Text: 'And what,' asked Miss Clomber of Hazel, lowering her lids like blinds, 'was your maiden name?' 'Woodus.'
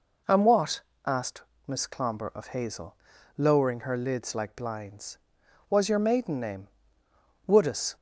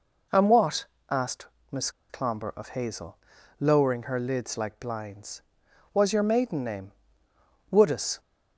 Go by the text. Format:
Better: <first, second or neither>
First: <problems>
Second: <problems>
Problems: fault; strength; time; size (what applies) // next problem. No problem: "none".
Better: first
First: pauses between "asked" and "Miss"; slight; at 1.4 s; 0.26 s long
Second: pauses between "asked" and "Miss"; slight; at 1.4 s; 0.26 s long // pauses between "Miss" and "Clomber"; slight; at 1.9 s; 0.19 s long